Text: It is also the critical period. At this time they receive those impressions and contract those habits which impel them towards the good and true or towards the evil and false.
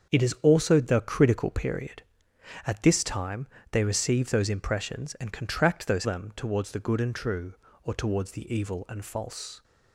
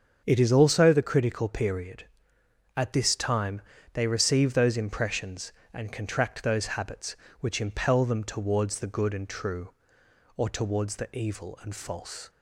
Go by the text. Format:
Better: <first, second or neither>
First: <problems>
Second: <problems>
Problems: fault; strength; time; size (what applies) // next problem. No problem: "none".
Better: second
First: starts louder than the rest; until 1.1 s; 7 dB // pauses between "time" and "they"; slight; at 3.4 s; 0.26 s long // skips "habits which impel"; at 6.0 s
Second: starts louder than the rest; strong; until 1.2 s; 7 dB // pauses between "time" and "they"; slight; at 3.5 s; 0.32 s long